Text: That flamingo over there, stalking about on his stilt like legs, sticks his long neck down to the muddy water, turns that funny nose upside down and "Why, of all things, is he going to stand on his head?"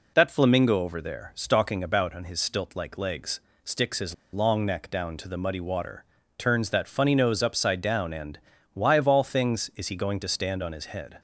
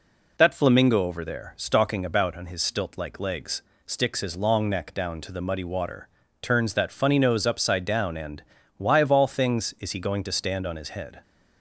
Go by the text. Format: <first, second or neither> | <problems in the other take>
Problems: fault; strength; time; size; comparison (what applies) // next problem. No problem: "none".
second | pauses between "his" and "long"; slight; at 4.1 s; 0.18 s long // pauses between "and" and "Why"; slight; at 8.3 s; 0.36 s long; slight in the second